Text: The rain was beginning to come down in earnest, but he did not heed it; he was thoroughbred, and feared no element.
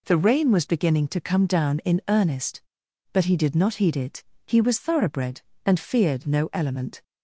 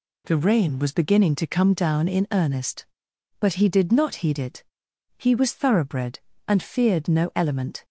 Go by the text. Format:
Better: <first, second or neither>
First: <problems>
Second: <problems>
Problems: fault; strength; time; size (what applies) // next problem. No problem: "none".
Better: neither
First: none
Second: none